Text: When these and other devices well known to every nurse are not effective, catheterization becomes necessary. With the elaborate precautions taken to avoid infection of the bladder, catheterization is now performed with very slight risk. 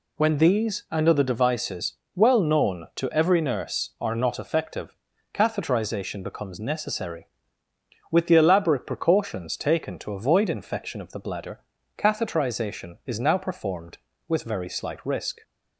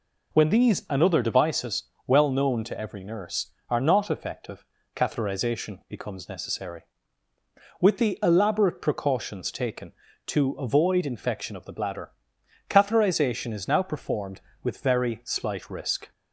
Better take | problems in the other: neither | pauses between "devices" and "well"; slight; the same in both

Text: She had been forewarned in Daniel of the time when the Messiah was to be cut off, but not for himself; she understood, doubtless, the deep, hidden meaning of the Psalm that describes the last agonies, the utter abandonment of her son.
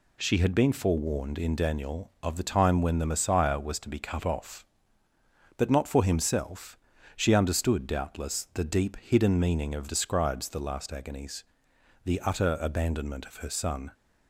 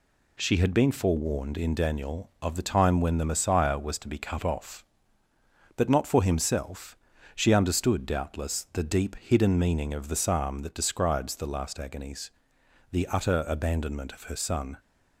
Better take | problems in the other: second | skips "the Psalm that"; at 9.8 s

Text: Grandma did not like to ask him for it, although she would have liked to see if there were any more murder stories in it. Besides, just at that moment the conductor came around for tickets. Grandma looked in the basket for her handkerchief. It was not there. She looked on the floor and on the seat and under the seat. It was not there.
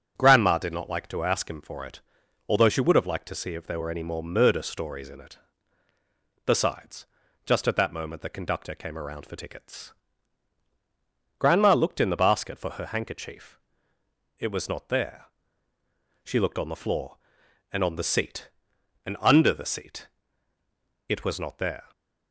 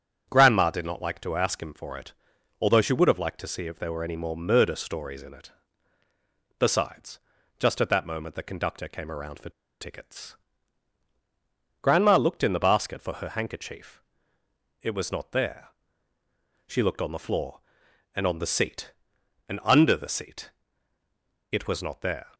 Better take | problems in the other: first | starts louder than the rest; strong; until 1.3 s; 7.5 dB; strong in the first // pauses between "for" and "tickets"; slight; at 9.4 s; 0.31 s long

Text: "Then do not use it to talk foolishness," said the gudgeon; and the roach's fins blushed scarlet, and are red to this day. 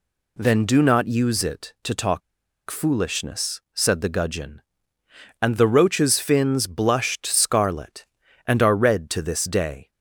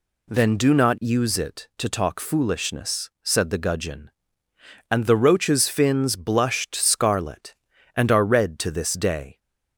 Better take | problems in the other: second | pauses between "talk" and "foolishness"; noticeable; at 2.2 s; 0.47 s long

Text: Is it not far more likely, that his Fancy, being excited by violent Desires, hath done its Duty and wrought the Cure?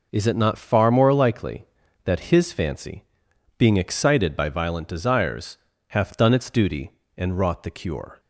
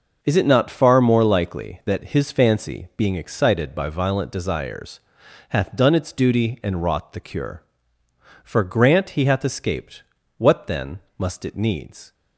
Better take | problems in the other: first | goes on to say "For grant he hath escaped what then must it needs"; strong; from 8.4 s on; 3.7 s long

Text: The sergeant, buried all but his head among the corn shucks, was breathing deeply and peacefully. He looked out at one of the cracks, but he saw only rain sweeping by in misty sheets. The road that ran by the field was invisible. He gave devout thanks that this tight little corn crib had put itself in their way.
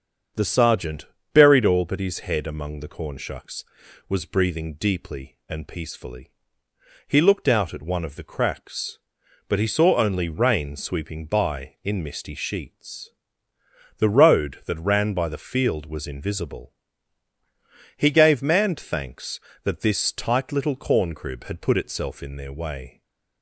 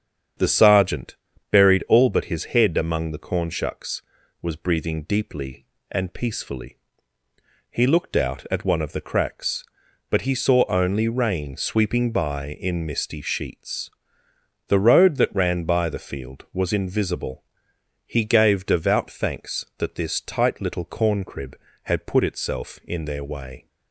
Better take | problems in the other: second | starts louder than the rest; until 1.6 s; 7 dB; strong in the second // says "manned" for "devout"; at 18.4 s // stays silent after the last word; slight; from 22.9 s on; 0.5 s long

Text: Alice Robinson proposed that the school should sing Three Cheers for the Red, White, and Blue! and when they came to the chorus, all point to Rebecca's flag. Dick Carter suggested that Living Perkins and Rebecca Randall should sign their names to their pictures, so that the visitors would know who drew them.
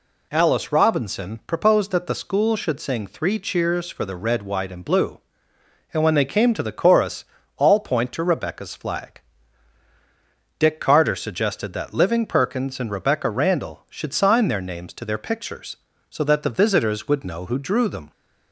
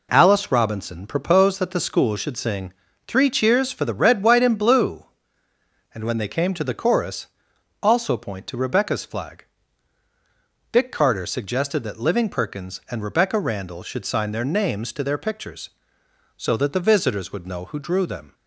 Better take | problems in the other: first | pauses between "sing" and "Three"; slight; at 2.7 s; 0.34 s long // says "also" for "all"; at 7.8 s

